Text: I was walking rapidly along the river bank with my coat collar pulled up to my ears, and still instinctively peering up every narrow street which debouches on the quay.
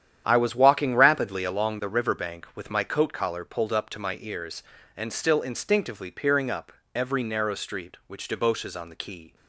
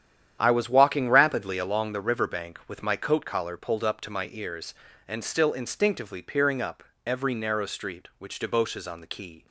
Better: neither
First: starts louder than the rest; strong; until 1.2 s; 9.5 dB // pauses between "up" and "every"; slight; at 6.7 s; 0.20 s long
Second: starts louder than the rest; strong; until 1.4 s; 9.5 dB // pauses between "up" and "every"; slight; at 6.8 s; 0.20 s long

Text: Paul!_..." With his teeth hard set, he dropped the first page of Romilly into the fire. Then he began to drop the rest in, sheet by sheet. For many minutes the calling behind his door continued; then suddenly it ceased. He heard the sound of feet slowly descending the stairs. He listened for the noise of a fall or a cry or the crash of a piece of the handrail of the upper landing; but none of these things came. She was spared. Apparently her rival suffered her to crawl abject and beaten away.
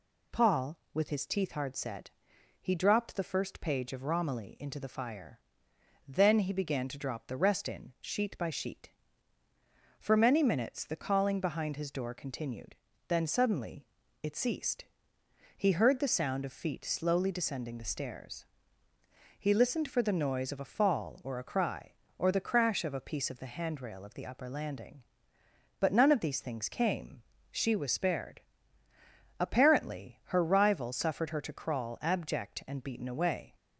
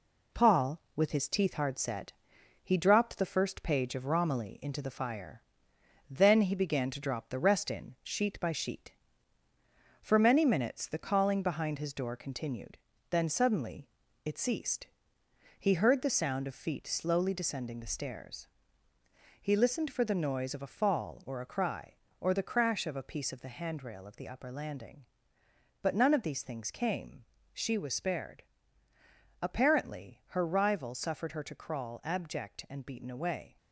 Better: first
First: pauses between "suddenly" and "it"; at 13.8 s; 0.38 s long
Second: gets quieter; noticeable; throughout; 4.5 dB // pauses between "suddenly" and "it"; at 13.8 s; 0.38 s long

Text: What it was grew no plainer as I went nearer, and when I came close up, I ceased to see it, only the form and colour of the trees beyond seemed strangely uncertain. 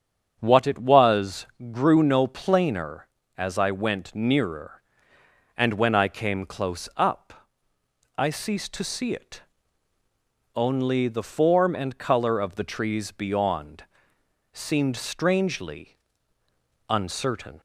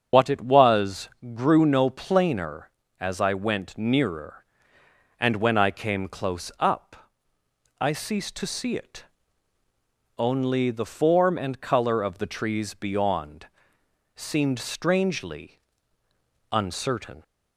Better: first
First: starts louder than the rest; strong; until 1.4 s; 8 dB // pauses between "was" and "grew"; slight; at 1.4 s; 0.26 s long // pauses between "beyond" and "seemed"; noticeable; at 13.8 s; 0.68 s long // pauses between "strangely" and "uncertain"; noticeable; at 15.9 s; 0.92 s long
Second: loses the start of "What"; at 0.1 s; 105 ms // starts louder than the rest; strong; until 1.4 s; 7 dB // pauses between "was" and "grew"; slight; at 1.0 s; 0.26 s long // pauses between "beyond" and "seemed"; noticeable; at 13.4 s; 0.68 s long // pauses between "strangely" and "uncertain"; noticeable; at 15.5 s; 0.92 s long

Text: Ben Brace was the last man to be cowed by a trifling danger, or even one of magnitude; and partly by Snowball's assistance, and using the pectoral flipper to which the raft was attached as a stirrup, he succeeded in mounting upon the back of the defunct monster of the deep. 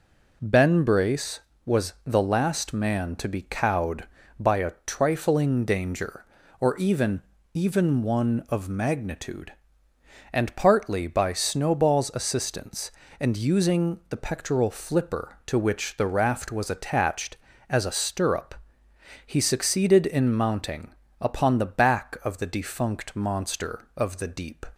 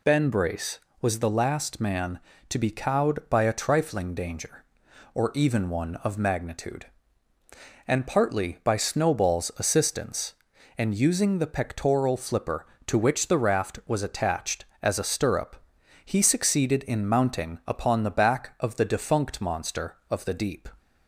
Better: second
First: says "even" twice; at 7.5 s // pauses between "mounting" and "upon"; slight; at 20.9 s; 0.26 s long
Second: none

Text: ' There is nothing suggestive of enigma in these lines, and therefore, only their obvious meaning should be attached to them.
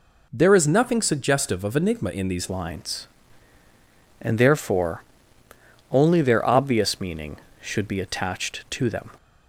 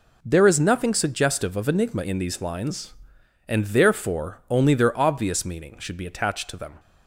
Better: second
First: changes voice at "lines"; from 2.4 s on; 6.6 s long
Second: none

